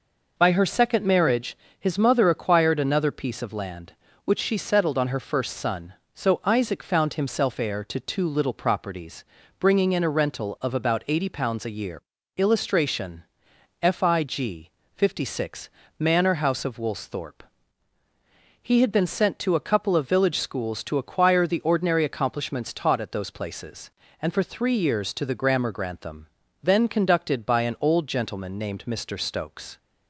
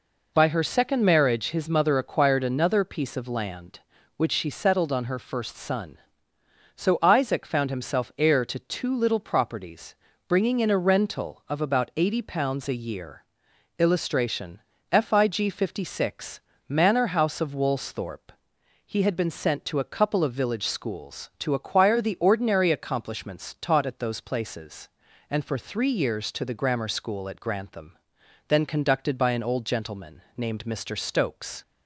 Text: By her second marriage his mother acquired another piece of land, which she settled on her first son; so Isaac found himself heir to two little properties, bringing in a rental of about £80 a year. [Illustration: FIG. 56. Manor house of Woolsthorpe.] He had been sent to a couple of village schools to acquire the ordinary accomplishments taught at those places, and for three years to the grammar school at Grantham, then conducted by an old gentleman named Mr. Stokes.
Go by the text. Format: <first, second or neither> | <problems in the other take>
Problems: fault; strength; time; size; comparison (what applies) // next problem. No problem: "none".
second | pauses between "marriage" and "his"; slight; at 1.5 s; 0.22 s long // skips "school at"; at 25.7 s